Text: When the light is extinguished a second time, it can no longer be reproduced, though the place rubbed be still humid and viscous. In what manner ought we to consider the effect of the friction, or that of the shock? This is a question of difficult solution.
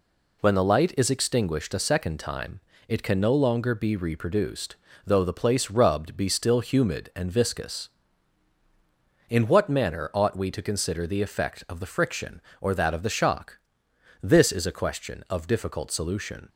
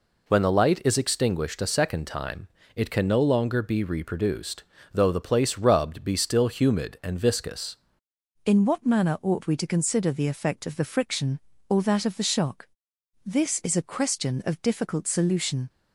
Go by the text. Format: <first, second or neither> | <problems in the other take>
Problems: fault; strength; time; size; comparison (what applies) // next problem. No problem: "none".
first | changes voice at "In"; from 8.4 s on; 7.2 s long